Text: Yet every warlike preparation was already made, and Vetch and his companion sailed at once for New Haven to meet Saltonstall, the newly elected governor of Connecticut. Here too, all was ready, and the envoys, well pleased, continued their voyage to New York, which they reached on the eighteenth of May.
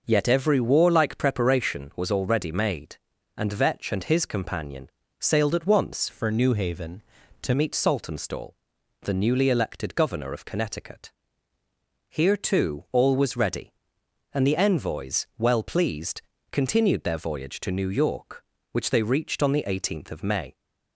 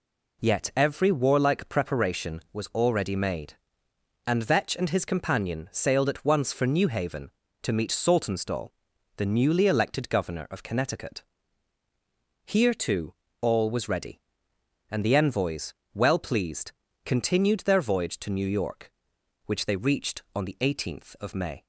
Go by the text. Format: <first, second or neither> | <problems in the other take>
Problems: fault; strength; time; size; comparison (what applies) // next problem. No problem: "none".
second | pauses between "companion" and "sailed"; slight; at 4.8 s; 0.30 s long // changes voice from "for" to "to"; from 6.0 to 7.5 s; 1.5 s long